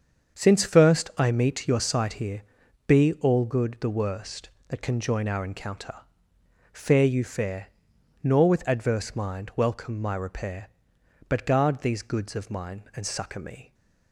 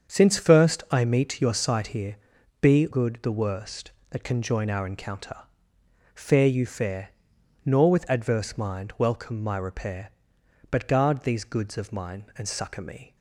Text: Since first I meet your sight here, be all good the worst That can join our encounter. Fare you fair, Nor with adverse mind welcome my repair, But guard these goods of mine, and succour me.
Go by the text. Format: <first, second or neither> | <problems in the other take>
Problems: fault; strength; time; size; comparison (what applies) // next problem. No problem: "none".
first | starts louder than the rest; until 1.1 s; 7 dB; strong in the first // skips "all"; at 2.8 s